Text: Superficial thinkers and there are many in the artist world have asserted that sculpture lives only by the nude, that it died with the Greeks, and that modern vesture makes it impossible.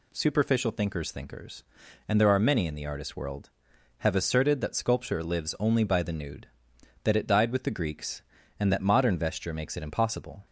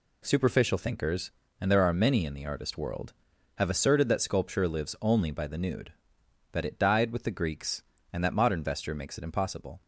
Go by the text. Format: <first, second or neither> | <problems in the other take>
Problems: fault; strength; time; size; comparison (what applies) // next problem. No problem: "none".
second | says "thinkers" twice; at 1.1 s